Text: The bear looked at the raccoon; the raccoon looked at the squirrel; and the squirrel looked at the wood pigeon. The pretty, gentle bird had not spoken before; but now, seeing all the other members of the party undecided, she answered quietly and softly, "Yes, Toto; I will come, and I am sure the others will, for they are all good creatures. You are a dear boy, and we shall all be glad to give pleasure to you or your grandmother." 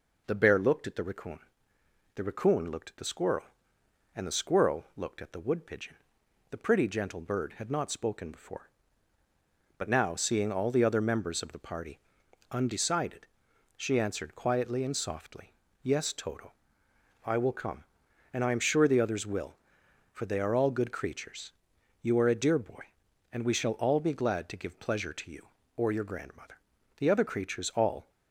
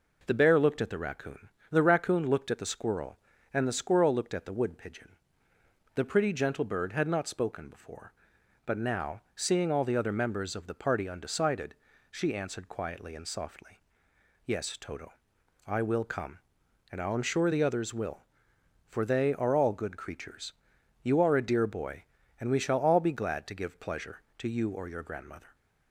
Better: second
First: pauses between "party" and "undecided"; noticeable; at 11.9 s; 0.54 s long // goes on to say "The other creatures all"; noticeable; from 26.9 s on; 1.1 s long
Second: none

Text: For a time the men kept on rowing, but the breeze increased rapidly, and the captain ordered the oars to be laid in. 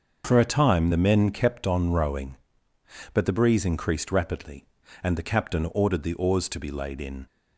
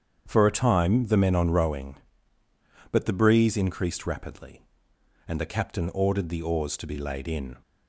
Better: first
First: starts louder than the rest; noticeable; until 1.2 s; 6 dB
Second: starts louder than the rest; strong; until 1.2 s; 7.5 dB // skips "kept"; at 1.3 s

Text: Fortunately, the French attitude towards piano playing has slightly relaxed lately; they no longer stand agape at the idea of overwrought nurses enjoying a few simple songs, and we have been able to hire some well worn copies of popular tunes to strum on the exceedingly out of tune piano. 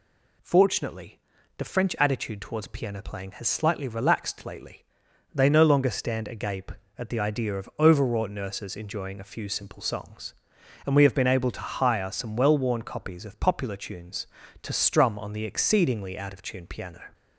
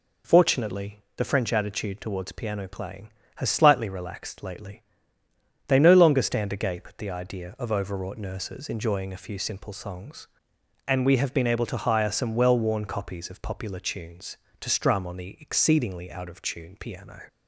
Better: neither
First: none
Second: none

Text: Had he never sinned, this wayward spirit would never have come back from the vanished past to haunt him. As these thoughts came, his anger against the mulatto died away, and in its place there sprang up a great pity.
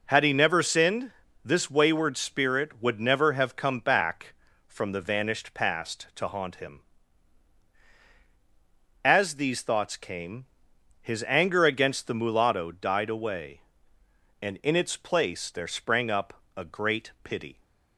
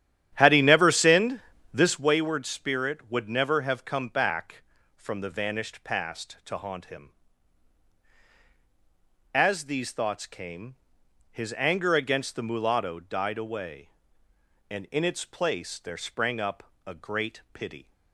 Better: first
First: pauses between "up" and "a"; slight; at 16.3 s; 0.24 s long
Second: starts louder than the rest; strong; until 2.2 s; 11 dB // pauses between "up" and "a"; slight; at 16.6 s; 0.24 s long

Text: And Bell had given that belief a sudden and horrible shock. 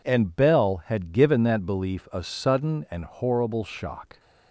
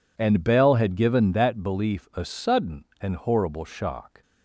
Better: neither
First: none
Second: none

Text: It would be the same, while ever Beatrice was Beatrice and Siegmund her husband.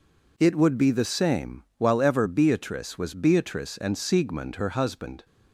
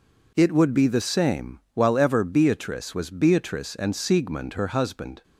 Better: neither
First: none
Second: none

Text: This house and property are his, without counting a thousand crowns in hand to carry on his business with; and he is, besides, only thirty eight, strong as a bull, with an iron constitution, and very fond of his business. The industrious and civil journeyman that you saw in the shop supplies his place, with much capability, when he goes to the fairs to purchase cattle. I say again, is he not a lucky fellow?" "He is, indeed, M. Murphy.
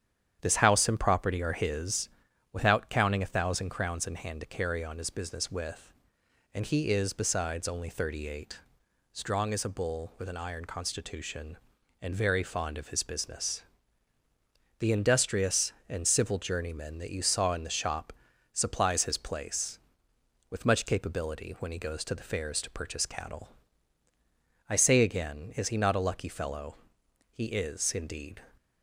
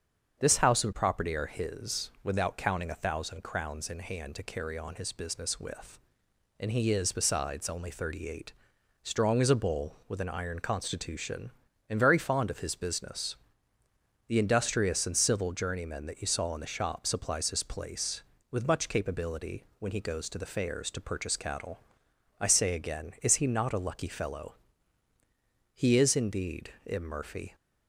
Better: second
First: starts louder than the rest; strong; until 1.4 s; 9 dB // pauses between "shop" and "supplies"; at 18.1 s; 0.40 s long // stops before "M Murphy"; at 28.5 s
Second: starts louder than the rest; strong; until 1.4 s; 7 dB

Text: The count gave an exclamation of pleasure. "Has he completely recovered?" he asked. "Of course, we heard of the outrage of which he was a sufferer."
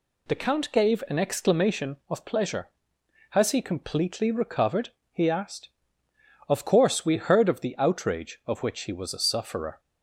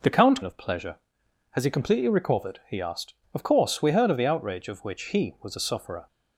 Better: first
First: none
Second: skips "gave an exclamation"; at 0.4 s

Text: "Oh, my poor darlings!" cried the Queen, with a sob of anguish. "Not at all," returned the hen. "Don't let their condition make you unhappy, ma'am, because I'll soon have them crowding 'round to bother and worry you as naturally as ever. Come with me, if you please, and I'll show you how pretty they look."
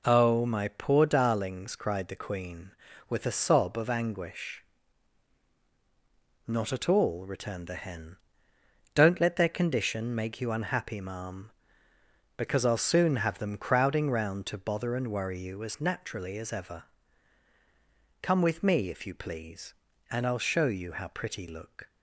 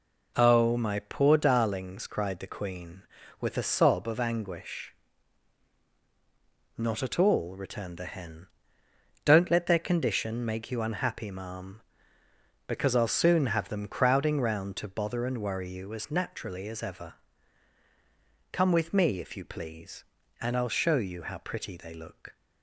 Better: second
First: skips "they"; at 21.4 s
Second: none

